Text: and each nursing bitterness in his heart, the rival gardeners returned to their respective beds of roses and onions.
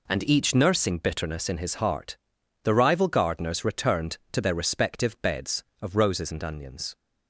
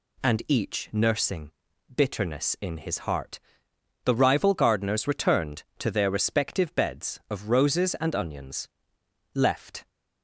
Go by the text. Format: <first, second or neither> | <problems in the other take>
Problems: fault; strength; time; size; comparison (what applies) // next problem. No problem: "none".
first | pauses between "nursing" and "bitterness"; at 1.5 s; 0.44 s long // goes on to say "Left"; from 9.3 s on; 0.54 s long